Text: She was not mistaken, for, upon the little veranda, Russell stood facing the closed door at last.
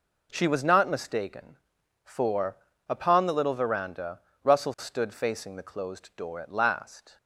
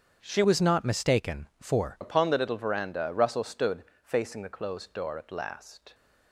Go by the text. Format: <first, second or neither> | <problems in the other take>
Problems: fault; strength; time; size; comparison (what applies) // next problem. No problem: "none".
first | starts louder than the rest; strong; until 1.2 s; 8 dB // changes voice from "was" to "for"; from 0.4 to 1.9 s; 1.5 s long // pauses between "stood" and "facing"; slight; at 3.8 s; 0.18 s long